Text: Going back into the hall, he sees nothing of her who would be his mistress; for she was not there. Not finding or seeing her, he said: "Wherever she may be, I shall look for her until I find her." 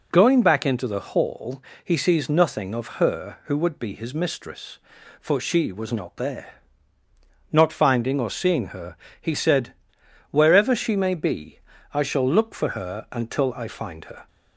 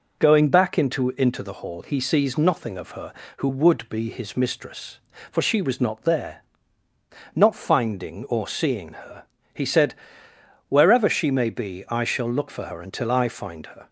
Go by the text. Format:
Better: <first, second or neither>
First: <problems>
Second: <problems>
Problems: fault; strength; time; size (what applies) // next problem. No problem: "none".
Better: first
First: none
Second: says "into" twice; at 1.1 s